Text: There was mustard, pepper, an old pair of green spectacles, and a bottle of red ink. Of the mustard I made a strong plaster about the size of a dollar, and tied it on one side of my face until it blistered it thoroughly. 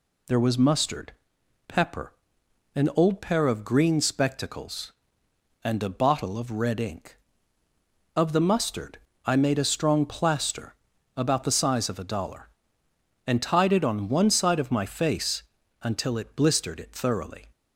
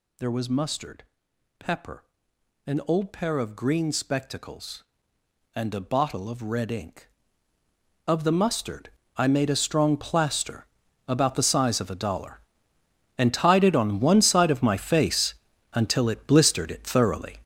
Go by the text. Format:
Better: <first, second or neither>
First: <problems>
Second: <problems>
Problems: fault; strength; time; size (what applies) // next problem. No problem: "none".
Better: first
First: pauses between "mustard" and "I"; slight; at 8.9 s; 0.26 s long // pauses between "plaster" and "about"; at 10.7 s; 0.42 s long // pauses between "face" and "until"; at 15.4 s; 0.40 s long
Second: gets louder; strong; throughout; 10 dB // pauses between "mustard" and "I"; slight; at 8.8 s; 0.26 s long // pauses between "plaster" and "about"; at 10.6 s; 0.42 s long // pauses between "face" and "until"; at 15.3 s; 0.40 s long